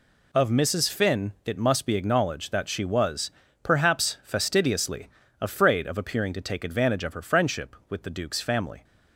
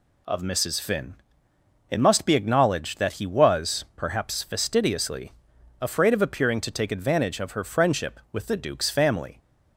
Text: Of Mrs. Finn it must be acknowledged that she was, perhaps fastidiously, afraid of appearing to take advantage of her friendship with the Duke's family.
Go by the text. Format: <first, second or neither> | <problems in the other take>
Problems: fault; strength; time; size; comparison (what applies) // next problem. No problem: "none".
first | pauses between "Finn" and "it"; noticeable; at 1.1 s; 0.74 s long // says "he" for "she"; at 3.1 s